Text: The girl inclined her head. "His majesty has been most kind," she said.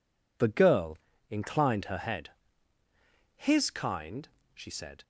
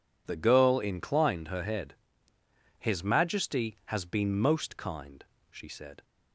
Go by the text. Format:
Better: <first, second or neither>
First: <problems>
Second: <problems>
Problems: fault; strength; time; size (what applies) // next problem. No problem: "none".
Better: second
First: pauses between "girl" and "inclined"; slight; at 0.9 s; 0.32 s long // skips "majesty has been most"; at 3.7 s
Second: none